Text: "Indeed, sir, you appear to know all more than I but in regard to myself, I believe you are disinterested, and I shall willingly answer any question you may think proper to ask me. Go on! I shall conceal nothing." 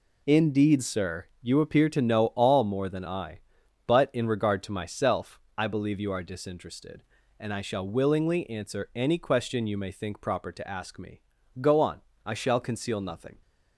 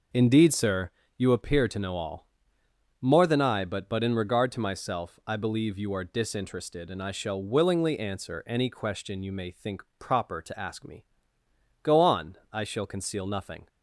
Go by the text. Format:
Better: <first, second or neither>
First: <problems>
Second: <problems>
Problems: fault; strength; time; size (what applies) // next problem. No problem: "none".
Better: first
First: none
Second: pauses between "all" and "more"; noticeable; at 2.2 s; 0.76 s long // says "but" twice; at 3.8 s // pauses between "think" and "proper"; slight; at 9.8 s; 0.16 s long